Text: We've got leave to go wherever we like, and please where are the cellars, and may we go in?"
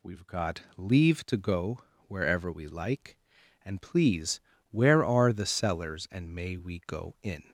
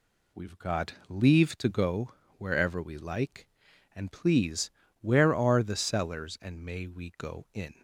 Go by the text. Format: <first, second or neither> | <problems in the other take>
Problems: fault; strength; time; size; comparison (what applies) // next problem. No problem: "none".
second | gets louder; slight; throughout; 2.5 dB // pauses between "go" and "wherever"; slight; at 1.8 s; 0.26 s long; slight in the second // pauses between "please" and "where"; slight; at 4.3 s; 0.30 s long; slight in the second